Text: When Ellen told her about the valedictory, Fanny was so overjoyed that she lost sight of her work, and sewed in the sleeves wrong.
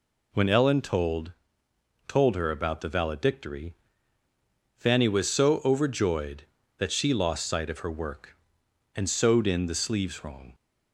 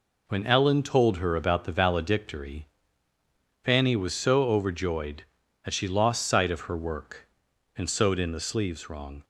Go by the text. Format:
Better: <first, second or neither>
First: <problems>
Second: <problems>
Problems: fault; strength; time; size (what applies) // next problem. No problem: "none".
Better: second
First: says "told" twice; at 2.0 s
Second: none